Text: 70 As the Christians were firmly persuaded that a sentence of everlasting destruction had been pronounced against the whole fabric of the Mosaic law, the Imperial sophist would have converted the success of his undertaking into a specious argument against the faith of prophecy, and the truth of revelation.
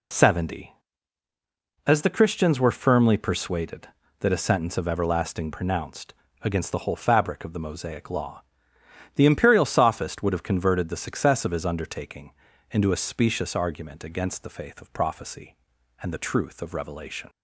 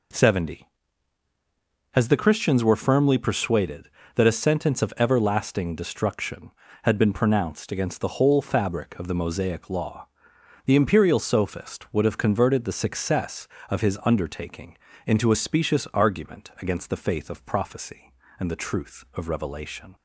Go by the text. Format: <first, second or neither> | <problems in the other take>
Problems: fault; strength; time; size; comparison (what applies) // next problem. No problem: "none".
second | skips "destruction had been"; at 5.5 s // pauses between "pronounced" and "against"; slight; at 6.1 s; 0.30 s long // pauses between "undertaking" and "into"; at 12.3 s; 0.40 s long; slight in the second